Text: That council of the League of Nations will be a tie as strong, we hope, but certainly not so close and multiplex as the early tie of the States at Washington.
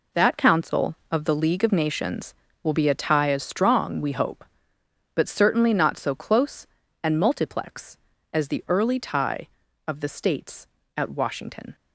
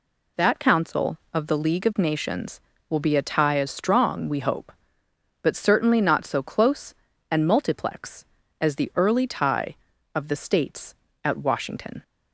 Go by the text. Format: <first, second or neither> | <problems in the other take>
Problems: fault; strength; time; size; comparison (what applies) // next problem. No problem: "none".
second | gets quieter; strong; throughout; 9.5 dB